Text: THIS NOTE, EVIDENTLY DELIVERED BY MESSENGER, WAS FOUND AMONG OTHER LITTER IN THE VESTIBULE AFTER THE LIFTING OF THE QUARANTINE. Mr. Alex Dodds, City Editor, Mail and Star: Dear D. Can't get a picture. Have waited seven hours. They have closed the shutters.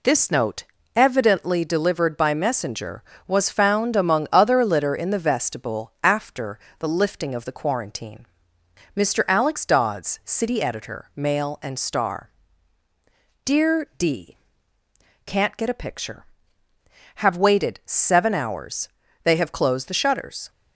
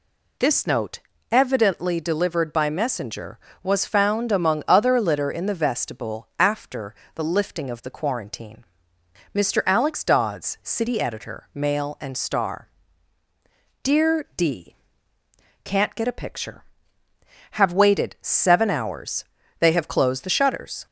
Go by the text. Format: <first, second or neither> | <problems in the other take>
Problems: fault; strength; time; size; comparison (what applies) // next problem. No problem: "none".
second | gets quieter; throughout; 4 dB // pauses between "AFTER" and "THE"; slight; at 6.5 s; 0.22 s long; slight in the second